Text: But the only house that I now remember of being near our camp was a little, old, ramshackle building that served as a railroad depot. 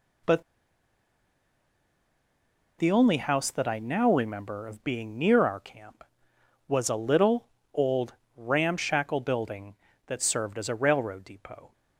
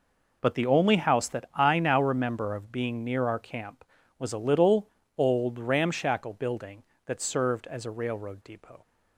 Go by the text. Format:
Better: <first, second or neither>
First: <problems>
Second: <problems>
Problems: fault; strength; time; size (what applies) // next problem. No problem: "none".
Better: second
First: pauses between "But" and "the"; strong; at 0.4 s; 2.3 s long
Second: none